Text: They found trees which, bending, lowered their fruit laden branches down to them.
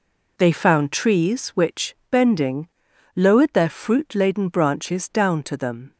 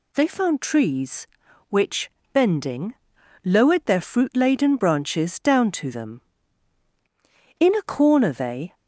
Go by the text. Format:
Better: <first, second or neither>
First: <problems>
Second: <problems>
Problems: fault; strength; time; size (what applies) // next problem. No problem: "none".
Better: first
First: none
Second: goes on to say "In a corner they"; noticeable; from 7.5 s on; 1.1 s long